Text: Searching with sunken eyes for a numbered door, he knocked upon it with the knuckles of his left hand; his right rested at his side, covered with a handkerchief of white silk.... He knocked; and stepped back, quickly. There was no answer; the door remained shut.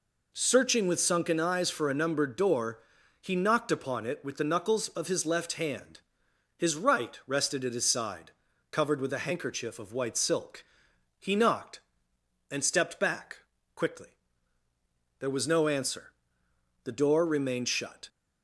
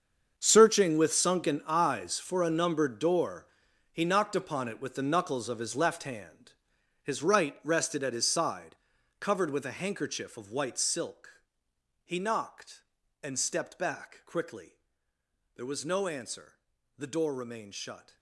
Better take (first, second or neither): first